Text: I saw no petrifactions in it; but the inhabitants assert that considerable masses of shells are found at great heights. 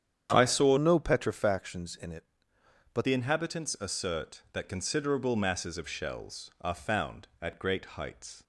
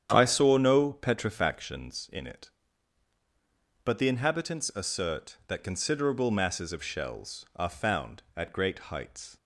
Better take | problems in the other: second | starts louder than the rest; strong; until 1.3 s; 9 dB; strong in the second // changes voice from "no" to "but"; from 0.7 to 3.0 s; 2.3 s long

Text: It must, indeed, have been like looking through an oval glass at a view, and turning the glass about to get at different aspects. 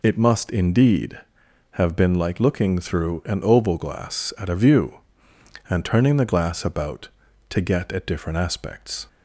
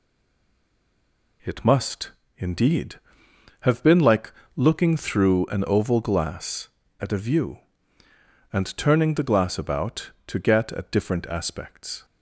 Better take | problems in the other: first | stays silent before the first word; noticeable; until 1.4 s; 1.4 s long // pauses between "like" and "looking"; slight; at 4.3 s; 0.24 s long

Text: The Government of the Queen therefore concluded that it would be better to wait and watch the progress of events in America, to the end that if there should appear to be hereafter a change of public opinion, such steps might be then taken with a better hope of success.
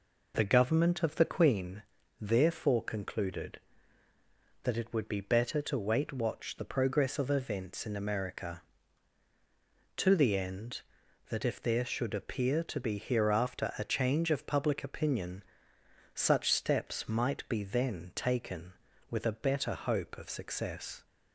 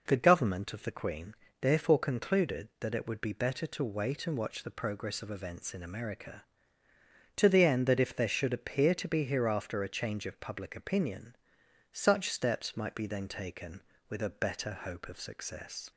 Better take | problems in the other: second | pauses between "Queen" and "therefore"; at 1.8 s; 0.38 s long; slight in the second // skips "and"; at 6.1 s

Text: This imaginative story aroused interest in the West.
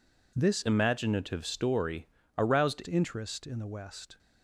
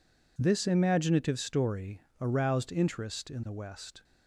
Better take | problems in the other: second | changes voice from "imaginative" to "aroused"; from 0.6 to 2.8 s; 2.2 s long // pauses between "story" and "aroused"; slight; at 2.0 s; 0.30 s long; slight in the second

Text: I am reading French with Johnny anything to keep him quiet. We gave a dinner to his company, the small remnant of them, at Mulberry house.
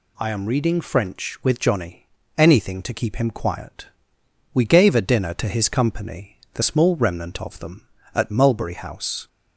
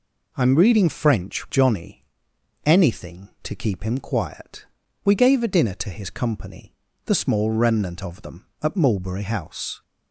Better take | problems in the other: first | skips "with"; at 1.4 s // pauses between "Johnny" and "anything"; noticeable; at 2.0 s; 0.62 s long; slight in the first

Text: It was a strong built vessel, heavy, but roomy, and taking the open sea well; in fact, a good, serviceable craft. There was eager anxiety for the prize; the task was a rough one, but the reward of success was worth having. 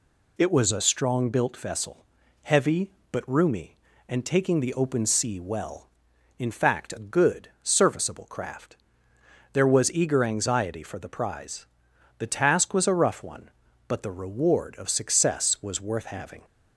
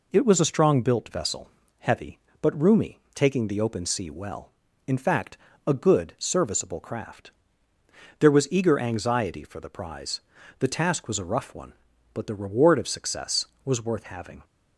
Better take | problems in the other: first | skips "and"; at 3.0 s

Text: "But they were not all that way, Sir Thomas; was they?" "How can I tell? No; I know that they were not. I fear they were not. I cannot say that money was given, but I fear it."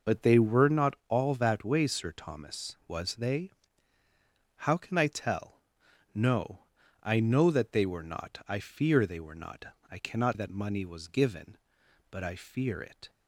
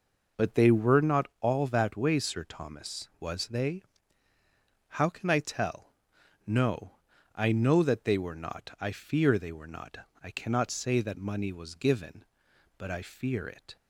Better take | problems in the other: second | skips "say"; at 10.3 s

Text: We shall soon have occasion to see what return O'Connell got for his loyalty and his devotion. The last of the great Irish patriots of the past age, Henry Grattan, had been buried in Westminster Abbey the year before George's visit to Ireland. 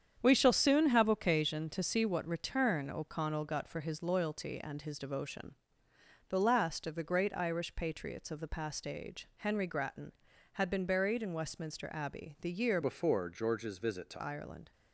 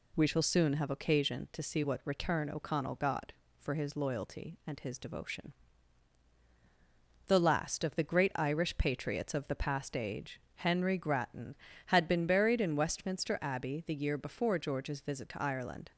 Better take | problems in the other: second | starts louder than the rest; strong; until 1.2 s; 8 dB // changes voice from "before" to "to"; from 12.8 to 14.2 s; 1.4 s long

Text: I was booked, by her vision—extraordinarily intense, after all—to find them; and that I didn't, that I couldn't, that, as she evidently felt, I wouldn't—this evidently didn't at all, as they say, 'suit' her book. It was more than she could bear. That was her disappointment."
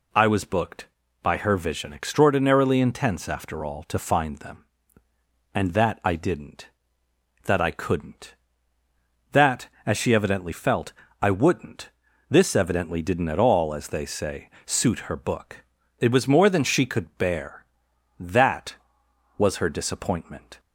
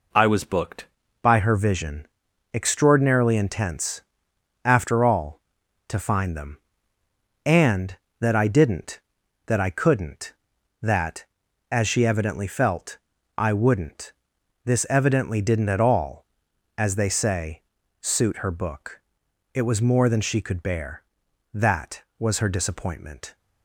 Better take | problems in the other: first | changes voice at "by"; from 1.2 s on; 22.1 s long

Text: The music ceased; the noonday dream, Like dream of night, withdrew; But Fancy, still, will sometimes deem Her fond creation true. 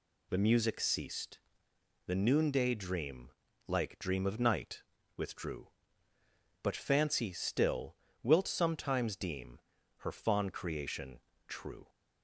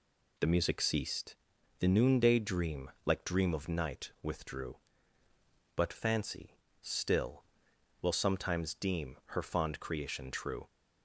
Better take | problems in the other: second | says "wilt" for "will"; at 8.2 s // pauses between "deem" and "Her"; at 9.5 s; 0.40 s long // pauses between "creation" and "true"; slight; at 11.2 s; 0.26 s long

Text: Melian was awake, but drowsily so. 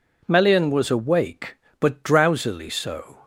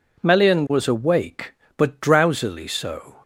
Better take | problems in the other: neither | none

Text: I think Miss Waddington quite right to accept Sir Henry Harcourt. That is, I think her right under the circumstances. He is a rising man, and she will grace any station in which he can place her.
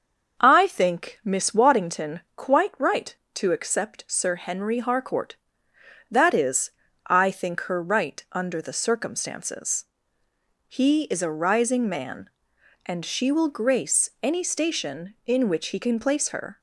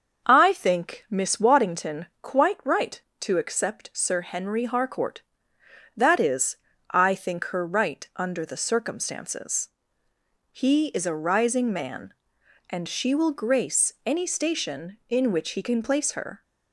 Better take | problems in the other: neither | starts louder than the rest; the same in both

